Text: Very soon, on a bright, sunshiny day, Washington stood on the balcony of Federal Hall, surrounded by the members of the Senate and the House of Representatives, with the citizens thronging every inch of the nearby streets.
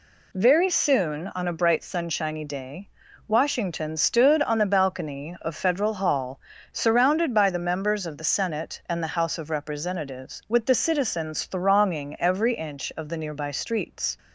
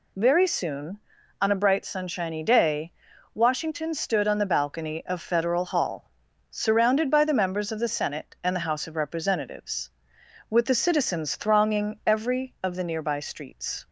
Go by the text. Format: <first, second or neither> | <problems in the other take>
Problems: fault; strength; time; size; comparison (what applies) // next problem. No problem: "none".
first | skips "inch"; at 12.5 s